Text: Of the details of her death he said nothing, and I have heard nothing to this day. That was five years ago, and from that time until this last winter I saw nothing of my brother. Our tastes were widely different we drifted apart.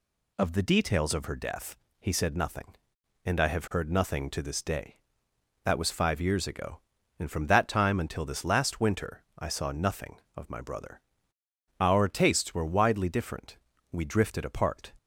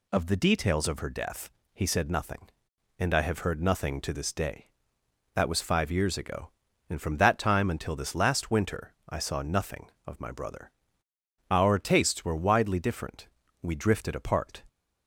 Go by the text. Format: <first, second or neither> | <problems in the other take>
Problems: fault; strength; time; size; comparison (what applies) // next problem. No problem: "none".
neither | pauses between "death" and "he"; slight; the same in both // pauses between "winter" and "I"; slight; the same in both // pauses between "different" and "we"; slight; the same in both